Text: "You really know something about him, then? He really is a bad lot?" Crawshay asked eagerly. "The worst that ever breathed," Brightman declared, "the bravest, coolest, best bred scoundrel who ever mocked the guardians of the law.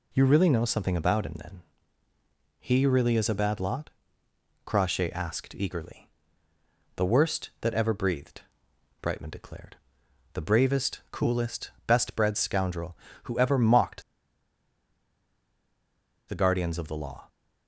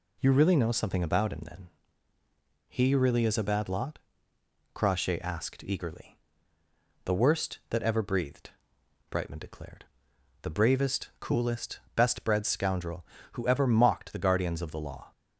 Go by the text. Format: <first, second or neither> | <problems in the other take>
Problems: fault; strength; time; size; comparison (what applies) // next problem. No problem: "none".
second | pauses between "mocked" and "the"; strong; at 14.0 s; 2.2 s long